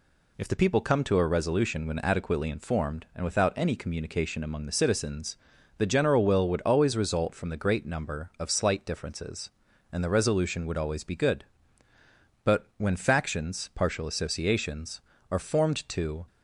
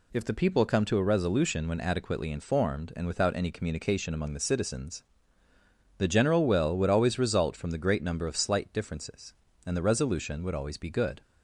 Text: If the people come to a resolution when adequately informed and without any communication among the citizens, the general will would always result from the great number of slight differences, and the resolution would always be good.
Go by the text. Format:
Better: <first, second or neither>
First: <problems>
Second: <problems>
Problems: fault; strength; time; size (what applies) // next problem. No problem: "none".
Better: second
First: goes on to say "But when factions partial associations are formed to"; strong; from 12.4 s on; 3.8 s long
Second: none